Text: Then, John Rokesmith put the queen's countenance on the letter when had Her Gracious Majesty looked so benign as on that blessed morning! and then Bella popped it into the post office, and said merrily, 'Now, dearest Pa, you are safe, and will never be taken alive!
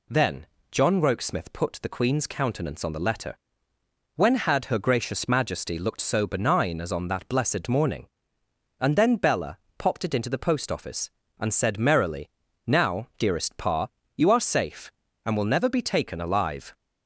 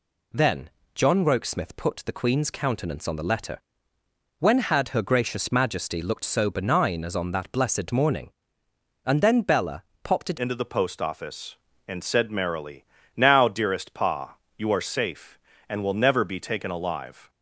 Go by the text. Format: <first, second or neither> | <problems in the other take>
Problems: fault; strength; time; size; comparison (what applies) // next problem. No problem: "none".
first | pauses between "letter" and "when"; noticeable; at 3.5 s; 0.80 s long; noticeable in the first // pauses between "Bella" and "popped"; slight; at 9.8 s; 0.18 s long; slight in the first // changes voice at "into"; from 10.3 s on; 6.9 s long